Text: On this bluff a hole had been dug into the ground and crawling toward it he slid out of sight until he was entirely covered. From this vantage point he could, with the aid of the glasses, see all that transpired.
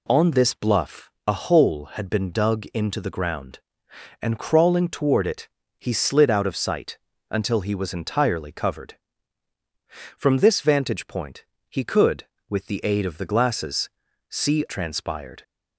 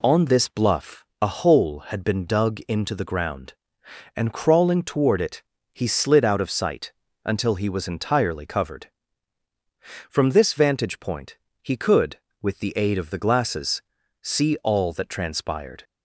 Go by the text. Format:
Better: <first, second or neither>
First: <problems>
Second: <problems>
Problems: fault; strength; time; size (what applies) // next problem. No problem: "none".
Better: second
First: pauses between "bluff" and "a"; slight; at 1.1 s; 0.16 s long // pauses between "it" and "he"; slight; at 5.4 s; 0.30 s long // pauses between "sight" and "until"; slight; at 6.9 s; 0.32 s long // pauses between "point" and "he"; slight; at 11.4 s; 0.24 s long // skips "all that"; at 14.6 s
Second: pauses between "bluff" and "a"; slight; at 1.0 s; 0.16 s long // pauses between "it" and "he"; slight; at 5.4 s; 0.30 s long // pauses between "sight" and "until"; slight; at 6.9 s; 0.32 s long // pauses between "point" and "he"; slight; at 11.3 s; 0.24 s long